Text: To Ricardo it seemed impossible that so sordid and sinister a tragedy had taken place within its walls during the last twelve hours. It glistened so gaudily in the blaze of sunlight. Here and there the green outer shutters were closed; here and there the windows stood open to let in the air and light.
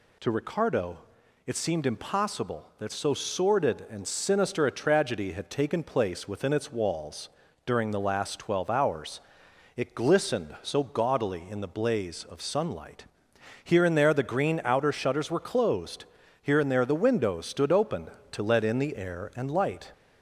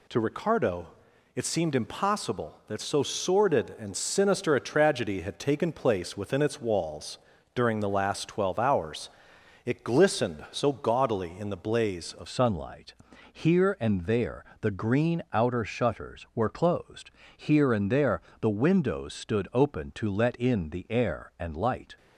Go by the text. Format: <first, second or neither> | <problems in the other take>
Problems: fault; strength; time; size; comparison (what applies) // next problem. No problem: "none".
first | pauses between "Ricardo" and "it"; noticeable; at 0.8 s; 0.46 s long; noticeable in the first // pauses between "walls" and "during"; slight; at 7.1 s; 0.36 s long; slight in the first // changes voice at "sunlight"; from 12.2 s on; 9.7 s long // pauses between "there" and "the"; slight; at 14.4 s; 0.16 s long // pauses between "there" and "the"; slight; at 18.2 s; 0.22 s long